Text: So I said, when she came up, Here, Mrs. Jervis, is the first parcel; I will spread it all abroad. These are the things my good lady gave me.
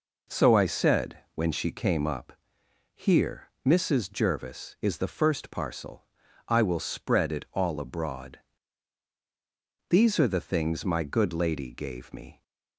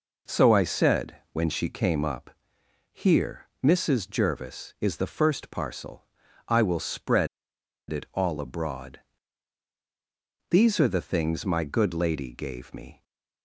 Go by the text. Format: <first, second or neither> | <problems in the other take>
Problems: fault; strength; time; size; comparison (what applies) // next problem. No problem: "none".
first | pauses between "spread" and "it"; noticeable; at 7.2 s; 0.63 s long